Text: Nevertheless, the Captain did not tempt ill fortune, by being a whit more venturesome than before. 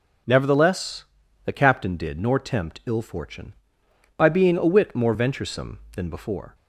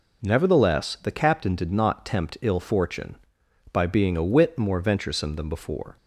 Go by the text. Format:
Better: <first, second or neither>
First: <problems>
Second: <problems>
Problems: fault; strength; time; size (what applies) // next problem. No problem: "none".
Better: second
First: says "nor" for "not"; at 2.1 s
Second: none